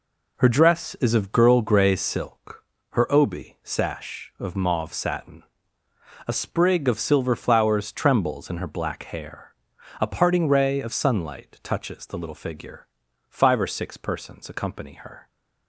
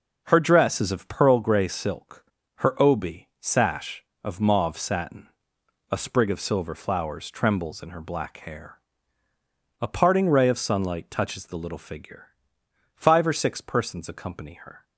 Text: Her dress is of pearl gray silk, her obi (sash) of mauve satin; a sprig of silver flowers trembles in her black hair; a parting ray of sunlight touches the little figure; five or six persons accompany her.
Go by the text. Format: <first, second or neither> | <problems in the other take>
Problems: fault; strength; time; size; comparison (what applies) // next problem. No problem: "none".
second | says "girl" for "pearl"; at 1.3 s